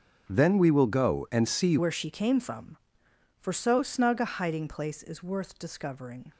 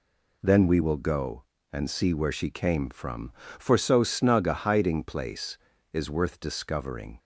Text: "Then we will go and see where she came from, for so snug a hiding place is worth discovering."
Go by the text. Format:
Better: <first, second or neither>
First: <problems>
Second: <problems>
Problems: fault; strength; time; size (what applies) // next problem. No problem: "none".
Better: second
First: starts louder than the rest; until 1.3 s; 6.5 dB // changes voice at "where"; from 1.7 s on; 4.6 s long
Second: none